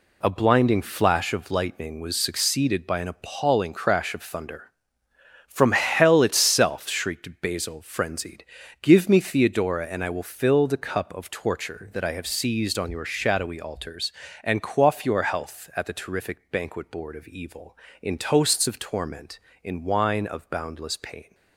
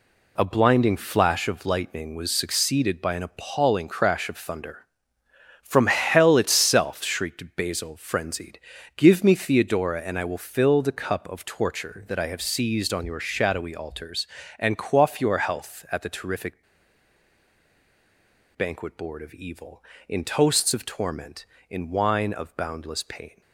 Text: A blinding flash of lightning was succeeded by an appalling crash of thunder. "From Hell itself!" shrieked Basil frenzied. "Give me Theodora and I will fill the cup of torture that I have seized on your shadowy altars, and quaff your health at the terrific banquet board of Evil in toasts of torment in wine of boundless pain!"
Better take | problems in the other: first | pauses between "terrific" and "banquet"; strong; at 16.6 s; 1.9 s long

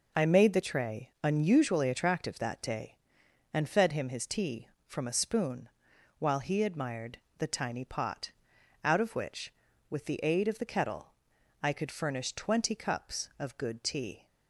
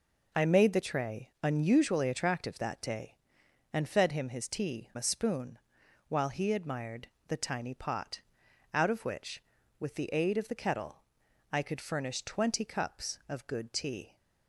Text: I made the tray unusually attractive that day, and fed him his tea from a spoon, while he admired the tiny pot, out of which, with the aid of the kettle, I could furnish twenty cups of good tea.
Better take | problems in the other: first | skips "from"; at 4.9 s // pauses between "admired" and "the"; slight; at 7.0 s; 0.20 s long; slight in the first

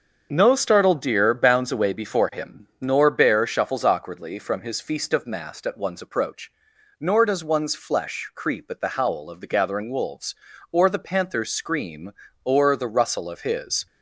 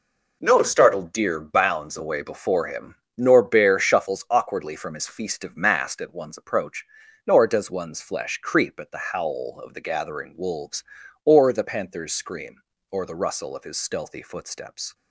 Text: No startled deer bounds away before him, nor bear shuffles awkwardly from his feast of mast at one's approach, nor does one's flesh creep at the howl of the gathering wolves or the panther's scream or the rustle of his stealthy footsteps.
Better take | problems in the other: second | starts louder than the rest; until 1.3 s; 6.5 dB // stops before "stealthy footsteps"; at 13.8 s

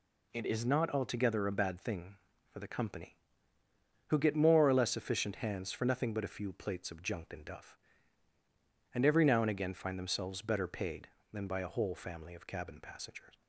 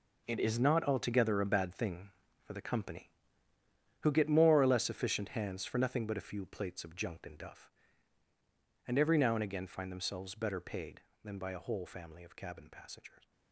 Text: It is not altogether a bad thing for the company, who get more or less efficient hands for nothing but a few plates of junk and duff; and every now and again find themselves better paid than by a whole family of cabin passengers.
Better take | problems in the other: first | gets quieter; strong; throughout; 12 dB

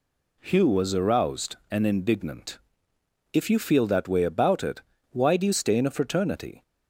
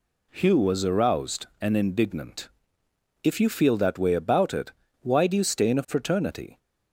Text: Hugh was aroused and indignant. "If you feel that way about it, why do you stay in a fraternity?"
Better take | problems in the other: neither | none

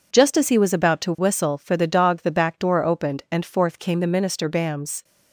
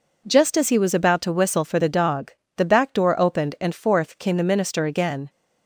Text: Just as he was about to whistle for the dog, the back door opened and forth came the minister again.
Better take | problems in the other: second | says "bams" for "again"; at 4.4 s

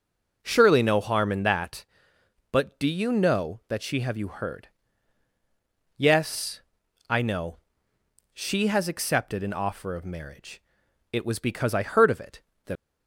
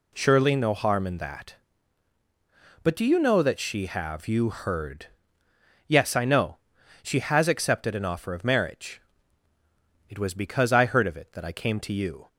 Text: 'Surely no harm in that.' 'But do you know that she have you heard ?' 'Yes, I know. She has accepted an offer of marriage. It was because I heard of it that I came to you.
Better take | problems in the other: second | starts louder than the rest; until 1.4 s; 7 dB // stops before "I came to you"; at 12.7 s

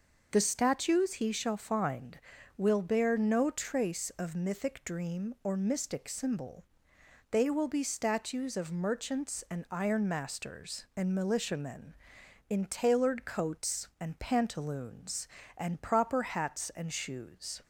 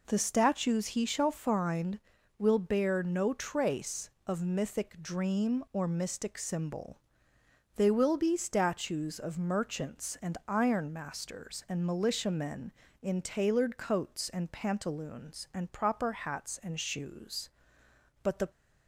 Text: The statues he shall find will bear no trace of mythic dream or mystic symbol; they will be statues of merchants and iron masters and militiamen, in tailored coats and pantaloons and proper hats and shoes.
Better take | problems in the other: first | goes on to say "But the"; slight; from 18.2 s on; 0.26 s long

